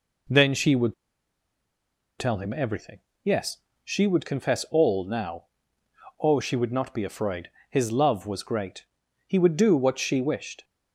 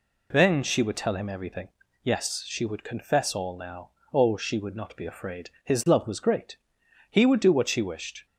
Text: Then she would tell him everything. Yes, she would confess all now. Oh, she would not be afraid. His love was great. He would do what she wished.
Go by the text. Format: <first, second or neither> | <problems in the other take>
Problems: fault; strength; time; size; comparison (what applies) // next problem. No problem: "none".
second | pauses between "would" and "tell"; strong; at 0.9 s; 1.2 s long